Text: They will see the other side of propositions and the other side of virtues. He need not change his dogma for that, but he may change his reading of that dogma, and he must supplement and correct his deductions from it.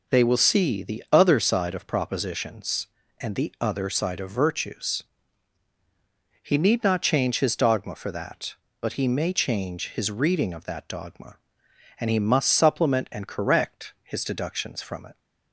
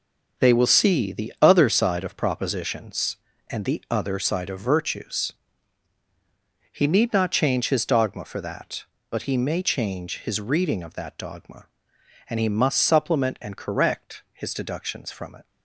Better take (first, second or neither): first